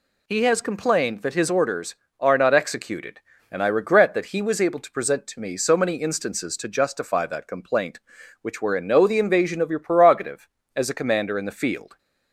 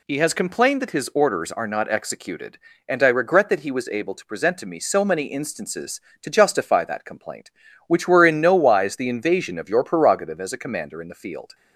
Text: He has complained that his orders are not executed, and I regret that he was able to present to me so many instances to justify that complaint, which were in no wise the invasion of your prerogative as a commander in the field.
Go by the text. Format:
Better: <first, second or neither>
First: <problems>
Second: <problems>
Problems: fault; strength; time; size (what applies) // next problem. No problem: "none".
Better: second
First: skips "wise"; at 9.0 s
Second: none